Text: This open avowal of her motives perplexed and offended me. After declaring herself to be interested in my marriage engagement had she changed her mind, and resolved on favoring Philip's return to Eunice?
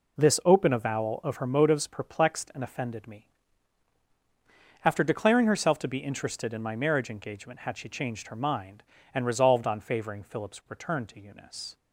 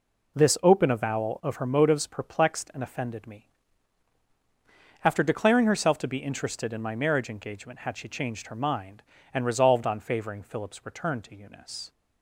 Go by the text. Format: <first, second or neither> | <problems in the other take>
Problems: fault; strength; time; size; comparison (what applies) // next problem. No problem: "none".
neither | none